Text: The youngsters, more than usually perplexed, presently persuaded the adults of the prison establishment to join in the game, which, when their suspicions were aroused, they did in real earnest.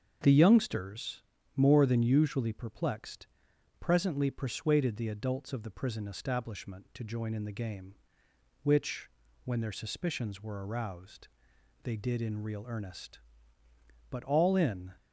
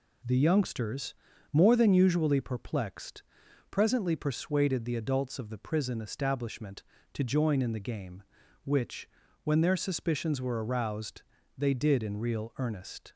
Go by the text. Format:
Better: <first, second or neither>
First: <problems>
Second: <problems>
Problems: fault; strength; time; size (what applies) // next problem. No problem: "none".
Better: second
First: starts louder than the rest; until 1.5 s; 7 dB // goes on to say "But all in"; noticeable; from 14.1 s on; 0.80 s long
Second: none